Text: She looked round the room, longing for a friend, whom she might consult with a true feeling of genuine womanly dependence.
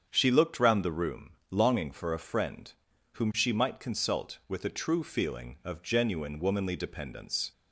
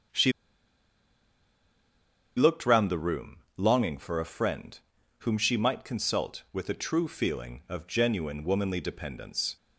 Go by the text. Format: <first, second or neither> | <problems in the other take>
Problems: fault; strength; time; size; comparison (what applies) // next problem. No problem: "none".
first | starts louder than the rest; strong; until 3.1 s; 7.5 dB; strong in the first // pauses between "She" and "looked"; strong; at 0.3 s; 2.0 s long